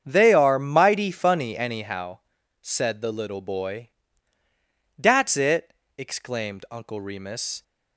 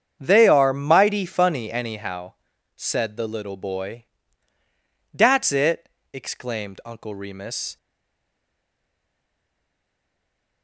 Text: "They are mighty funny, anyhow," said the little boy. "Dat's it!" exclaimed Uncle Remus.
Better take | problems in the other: first | starts louder than the rest; strong; until 1.2 s; 7.5 dB; strong in the first // stays silent after the last word; strong; from 7.7 s on; 2.9 s long

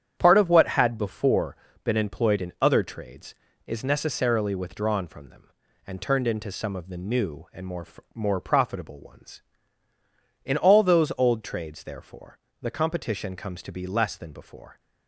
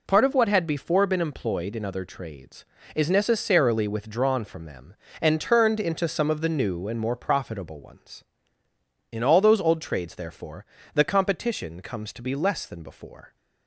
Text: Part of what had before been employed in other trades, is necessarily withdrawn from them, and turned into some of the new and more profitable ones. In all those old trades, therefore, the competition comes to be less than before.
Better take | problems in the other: second | starts louder than the rest; strong; until 1.1 s; 9 dB // pauses between "before" and "been"; slight; at 1.5 s; 0.30 s long // says "more" twice; at 8.1 s

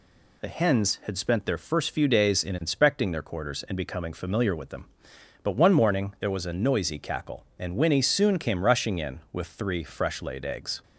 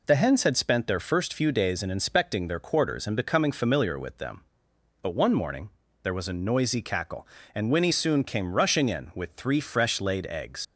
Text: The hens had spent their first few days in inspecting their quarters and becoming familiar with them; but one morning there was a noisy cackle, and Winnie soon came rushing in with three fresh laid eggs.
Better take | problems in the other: first | pauses between "morning" and "there"; slight; at 5.6 s; 0.32 s long // leaves "eggs" unfinished; at 10.6 s; 70 ms

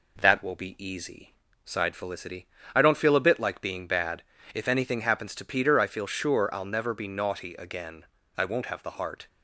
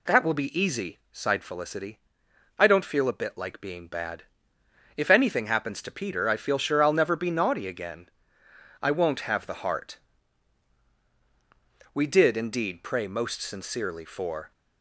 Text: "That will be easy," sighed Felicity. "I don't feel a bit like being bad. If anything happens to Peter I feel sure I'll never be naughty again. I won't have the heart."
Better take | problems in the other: first | goes on to say "We did indeed pray most sincerely for"; strong; from 11.9 s on; 2.5 s long

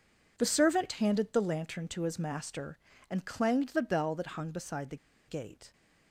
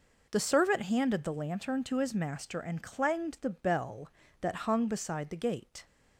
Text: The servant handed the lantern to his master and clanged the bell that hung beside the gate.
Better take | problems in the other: second | pauses between "the" and "gate"; slight; at 4.9 s; 0.31 s long

